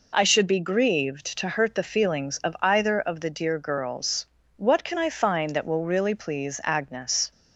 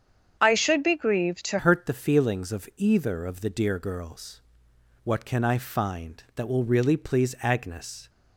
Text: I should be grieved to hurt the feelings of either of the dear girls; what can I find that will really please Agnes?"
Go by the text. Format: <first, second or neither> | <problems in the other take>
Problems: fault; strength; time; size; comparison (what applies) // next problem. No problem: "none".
first | starts louder than the rest; strong; until 1.4 s; 8 dB // changes voice at "hurt"; from 1.5 s on; 6.5 s long